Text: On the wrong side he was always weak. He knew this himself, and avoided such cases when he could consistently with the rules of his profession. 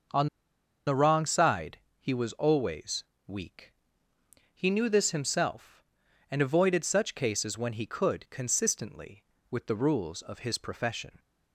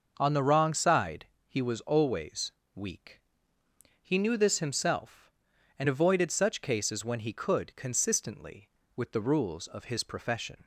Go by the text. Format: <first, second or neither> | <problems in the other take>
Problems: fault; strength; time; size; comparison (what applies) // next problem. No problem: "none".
second | starts louder than the rest; noticeable; until 1.7 s; 6 dB; noticeable in the second // pauses between "On" and "the"; noticeable; at 0.2 s; 0.60 s long // pauses between "side" and "he"; slight; at 1.7 s; 0.22 s long; slight in the second // pauses between "always" and "weak"; slight; at 3.0 s; 0.20 s long; slight in the second